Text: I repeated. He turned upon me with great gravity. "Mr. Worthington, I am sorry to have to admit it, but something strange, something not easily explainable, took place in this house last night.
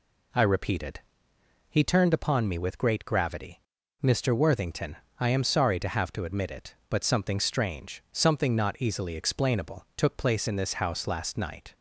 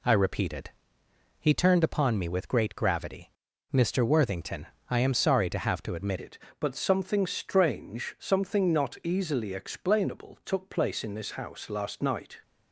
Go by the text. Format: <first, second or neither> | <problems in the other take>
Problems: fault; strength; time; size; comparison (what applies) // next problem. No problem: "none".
first | changes voice at "it"; from 6.1 s on; 6.3 s long